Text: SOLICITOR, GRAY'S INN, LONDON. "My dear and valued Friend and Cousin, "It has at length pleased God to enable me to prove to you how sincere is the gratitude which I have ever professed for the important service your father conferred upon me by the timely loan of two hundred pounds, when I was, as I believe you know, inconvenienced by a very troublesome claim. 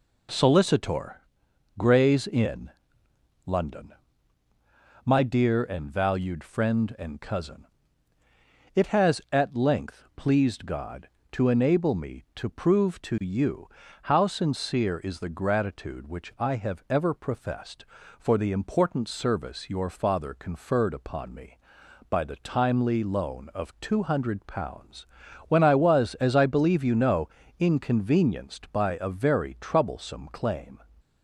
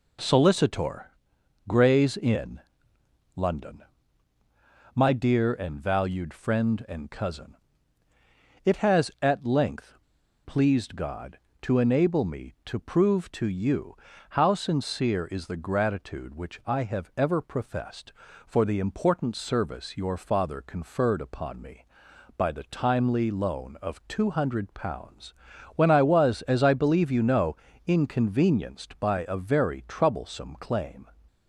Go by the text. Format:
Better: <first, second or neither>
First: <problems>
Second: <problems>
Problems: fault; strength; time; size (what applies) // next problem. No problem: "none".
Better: first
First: pauses between "you" and "how"; slight; at 13.6 s; 0.36 s long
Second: pauses between "length" and "pleased"; noticeable; at 9.9 s; 0.50 s long // pauses between "you" and "how"; slight; at 13.9 s; 0.36 s long